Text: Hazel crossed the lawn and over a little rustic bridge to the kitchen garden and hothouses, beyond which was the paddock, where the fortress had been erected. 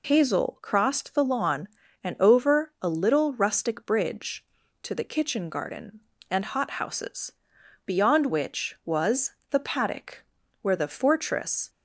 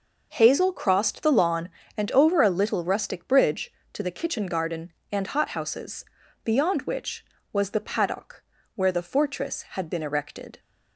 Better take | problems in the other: second | pauses between "was" and "the"; slight; at 9.3 s; 0.20 s long // stops before "had been erected"; at 11.6 s

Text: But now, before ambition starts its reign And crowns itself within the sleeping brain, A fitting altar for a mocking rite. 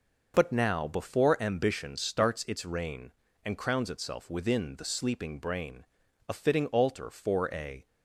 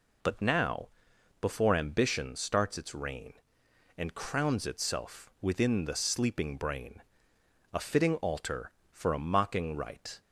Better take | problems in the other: second | stops before "mocking rite"; at 7.8 s

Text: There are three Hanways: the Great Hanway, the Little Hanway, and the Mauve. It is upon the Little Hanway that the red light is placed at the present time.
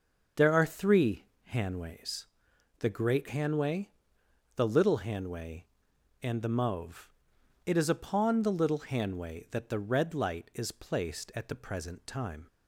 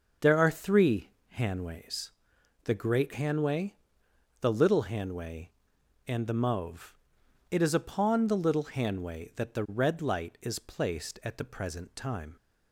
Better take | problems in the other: neither | starts louder than the rest; the same in both // pauses between "three" and "Hanways"; slight; the same in both

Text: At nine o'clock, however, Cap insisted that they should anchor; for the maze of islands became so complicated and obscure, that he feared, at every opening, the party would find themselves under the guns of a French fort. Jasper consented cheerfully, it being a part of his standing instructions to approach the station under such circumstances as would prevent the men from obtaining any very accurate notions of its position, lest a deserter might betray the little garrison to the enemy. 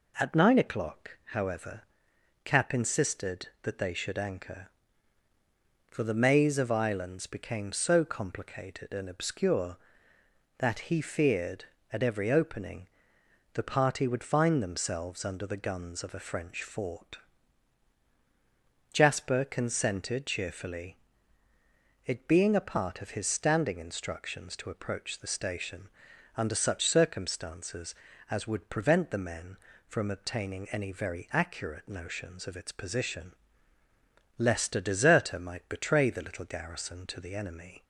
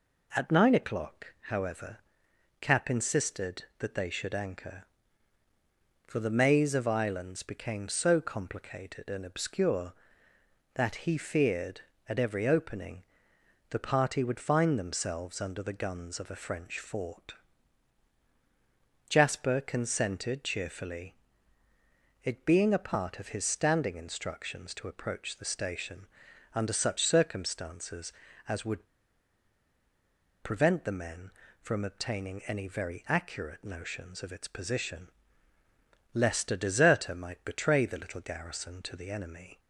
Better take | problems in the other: first | pauses between "station" and "under"; noticeable; at 26.0 s; 0.50 s long; noticeable in the first // pauses between "would" and "prevent"; strong; at 28.8 s; 1.5 s long

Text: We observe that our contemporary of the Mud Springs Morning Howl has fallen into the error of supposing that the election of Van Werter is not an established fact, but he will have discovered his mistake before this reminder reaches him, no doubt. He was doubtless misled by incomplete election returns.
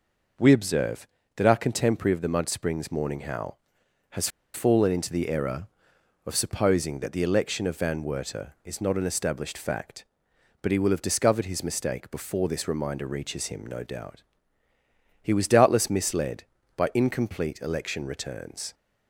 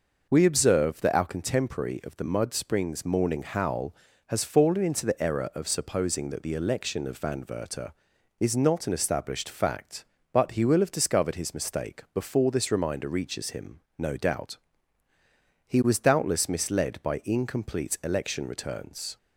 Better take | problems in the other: second | pauses between "has" and "fallen"; slight; at 4.2 s; 0.25 s long

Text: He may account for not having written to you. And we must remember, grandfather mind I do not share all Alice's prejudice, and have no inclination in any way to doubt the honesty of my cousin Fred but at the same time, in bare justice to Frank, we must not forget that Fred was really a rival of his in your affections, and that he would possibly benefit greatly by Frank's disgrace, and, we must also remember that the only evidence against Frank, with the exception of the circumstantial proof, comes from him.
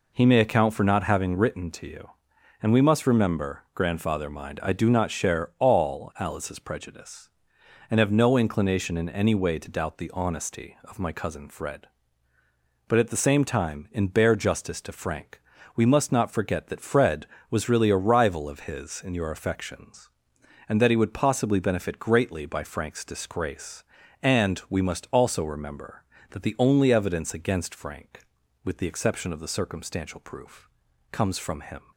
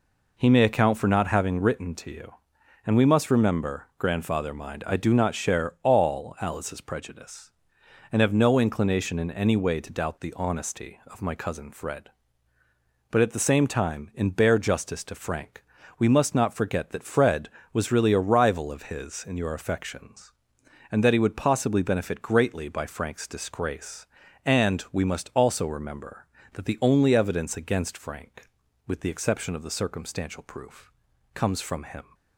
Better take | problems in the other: neither | none

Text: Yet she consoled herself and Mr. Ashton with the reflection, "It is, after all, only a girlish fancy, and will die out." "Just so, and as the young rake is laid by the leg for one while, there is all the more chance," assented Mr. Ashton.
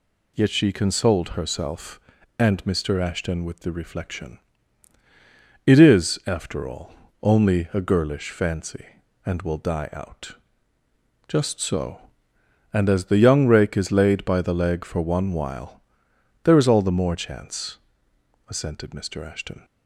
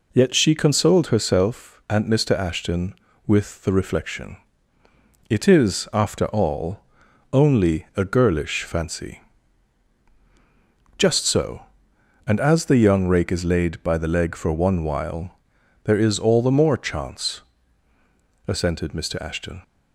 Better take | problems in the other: first | skips "and will die out"; at 10.0 s

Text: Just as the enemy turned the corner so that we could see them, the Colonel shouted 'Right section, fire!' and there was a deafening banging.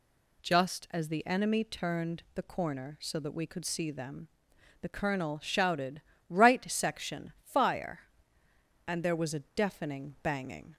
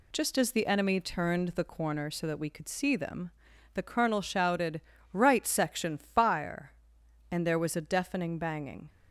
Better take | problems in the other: neither | pauses between "shouted" and "Right"; slight; the same in both

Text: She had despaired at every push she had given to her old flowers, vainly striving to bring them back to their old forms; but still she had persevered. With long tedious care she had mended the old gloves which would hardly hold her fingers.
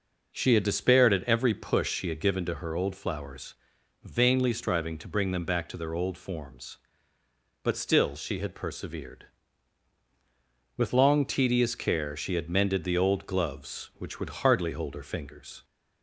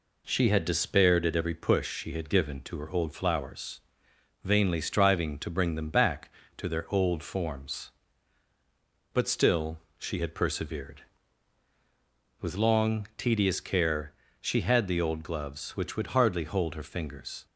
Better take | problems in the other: first | pauses between "still" and "she"; slight; at 9.7 s; 0.22 s long // pauses between "care" and "she"; slight; at 14.1 s; 0.28 s long // skips "mended"; at 14.8 s

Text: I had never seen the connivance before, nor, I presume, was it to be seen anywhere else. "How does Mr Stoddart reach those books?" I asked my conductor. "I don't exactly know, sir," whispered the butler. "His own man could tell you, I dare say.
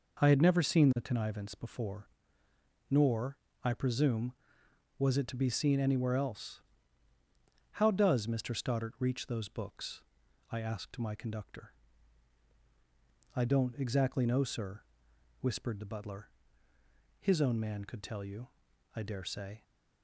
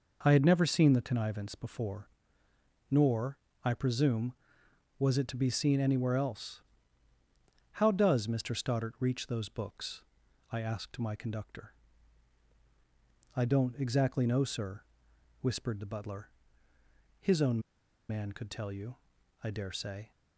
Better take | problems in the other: first | pauses between "own" and "man"; noticeable; at 17.5 s; 0.49 s long

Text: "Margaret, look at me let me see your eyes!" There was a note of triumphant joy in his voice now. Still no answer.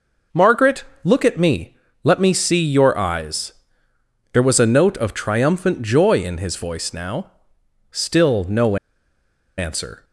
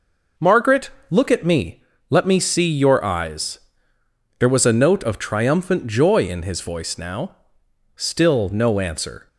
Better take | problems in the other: second | pauses between "me" and "let"; slight; at 1.7 s; 0.28 s long; slight in the second // pauses between "no" and "answer"; noticeable; at 8.7 s; 0.81 s long

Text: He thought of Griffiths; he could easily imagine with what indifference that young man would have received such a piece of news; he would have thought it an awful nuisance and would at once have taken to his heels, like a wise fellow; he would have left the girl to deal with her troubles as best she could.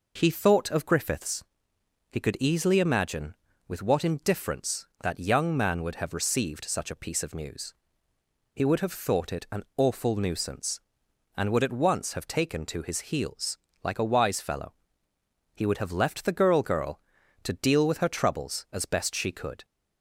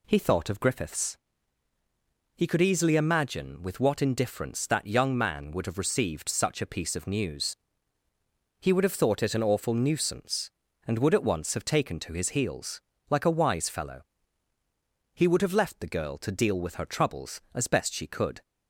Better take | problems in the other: second | says "girl" twice; at 16.6 s

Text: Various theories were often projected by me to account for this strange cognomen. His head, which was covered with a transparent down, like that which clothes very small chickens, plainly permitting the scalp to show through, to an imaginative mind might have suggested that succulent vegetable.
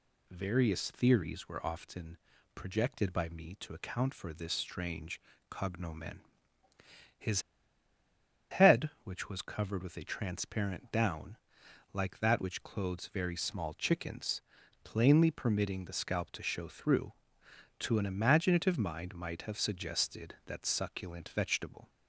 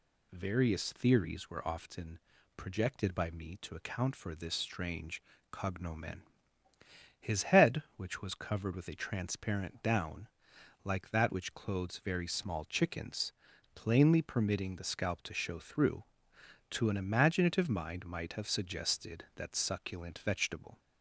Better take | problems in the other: second | pauses between "often" and "projected"; at 2.1 s; 0.38 s long; also in the second // pauses between "strange" and "cognomen"; slight; at 5.1 s; 0.30 s long; slight in the second // pauses between "His" and "head"; at 7.4 s; 1.0 s long

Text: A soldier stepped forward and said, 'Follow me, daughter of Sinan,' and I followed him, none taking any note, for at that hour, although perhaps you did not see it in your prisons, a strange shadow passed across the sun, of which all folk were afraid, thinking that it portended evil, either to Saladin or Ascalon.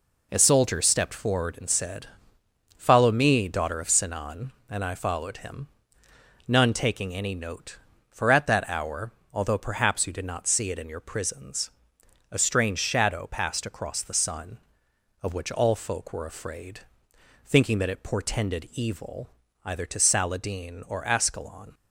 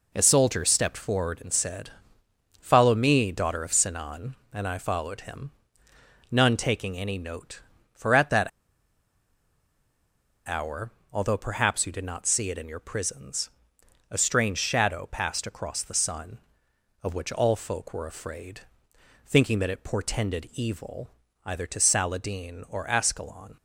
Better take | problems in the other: first | pauses between "that" and "hour"; strong; at 8.4 s; 1.9 s long

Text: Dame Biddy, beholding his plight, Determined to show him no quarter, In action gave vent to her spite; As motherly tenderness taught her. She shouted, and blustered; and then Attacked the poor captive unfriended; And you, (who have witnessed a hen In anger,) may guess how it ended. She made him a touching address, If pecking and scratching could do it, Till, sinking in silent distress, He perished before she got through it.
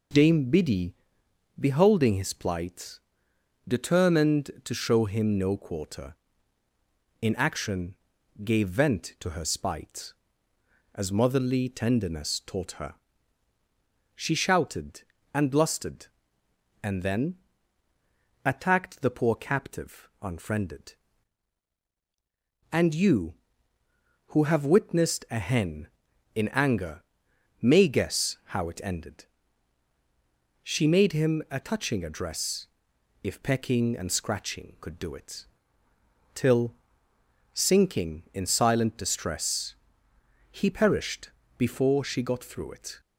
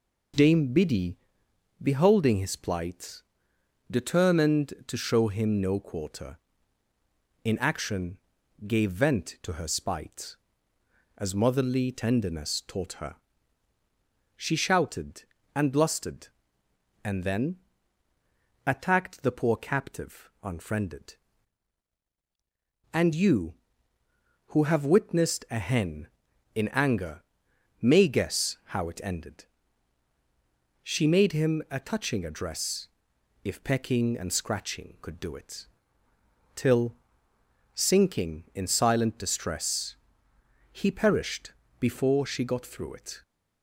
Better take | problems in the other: neither | pauses between "action" and "gave"; noticeable; the same in both // pauses between "then" and "Attacked"; the same in both // pauses between "perished" and "before"; slight; the same in both

